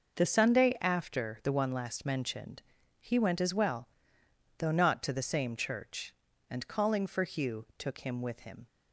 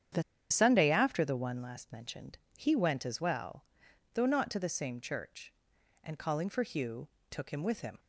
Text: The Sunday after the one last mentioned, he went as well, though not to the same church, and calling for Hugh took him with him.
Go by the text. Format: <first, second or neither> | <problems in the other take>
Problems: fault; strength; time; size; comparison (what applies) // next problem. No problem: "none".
first | starts louder than the rest; strong; until 1.4 s; 8.5 dB // pauses between "The" and "Sunday"; slight; at 0.2 s; 0.29 s long // pauses between "Hugh" and "took"; slight; at 7.0 s; 0.20 s long